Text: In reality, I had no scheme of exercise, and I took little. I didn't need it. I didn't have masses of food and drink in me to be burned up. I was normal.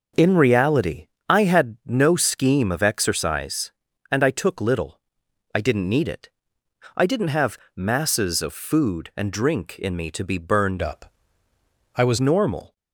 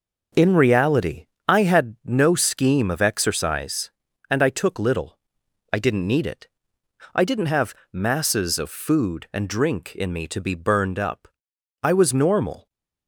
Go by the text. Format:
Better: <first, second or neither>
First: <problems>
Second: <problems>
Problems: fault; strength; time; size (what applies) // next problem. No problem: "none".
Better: second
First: starts louder than the rest; until 1.3 s; 6.5 dB // pauses between "have" and "masses"; slight; at 7.5 s; 0.16 s long // changes voice from "up" to "was"; from 10.8 to 12.1 s; 1.3 s long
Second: starts louder than the rest; until 1.5 s; 6 dB // pauses between "have" and "masses"; slight; at 7.7 s; 0.16 s long